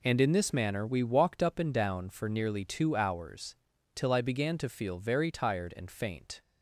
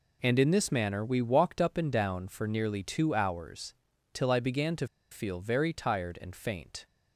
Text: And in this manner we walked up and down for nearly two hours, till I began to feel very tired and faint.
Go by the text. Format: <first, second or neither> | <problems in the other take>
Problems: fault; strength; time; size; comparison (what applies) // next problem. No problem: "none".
first | pauses between "to" and "feel"; slight; at 4.8 s; 0.25 s long